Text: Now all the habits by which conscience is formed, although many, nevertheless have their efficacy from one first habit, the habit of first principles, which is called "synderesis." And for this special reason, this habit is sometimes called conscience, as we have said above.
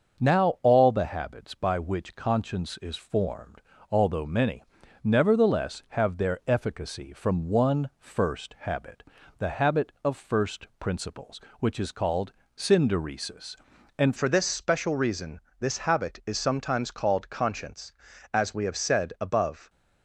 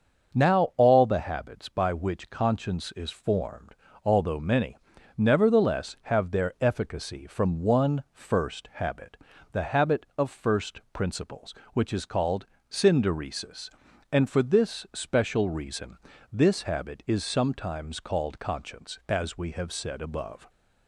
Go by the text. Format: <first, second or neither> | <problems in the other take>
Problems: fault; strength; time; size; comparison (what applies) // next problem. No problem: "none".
second | starts louder than the rest; until 1.2 s; 6.5 dB; also in the second // pauses between "called" and "synderesis"; slight; at 12.3 s; 0.26 s long; slight in the second // changes voice at "for"; from 14.1 s on; 5.5 s long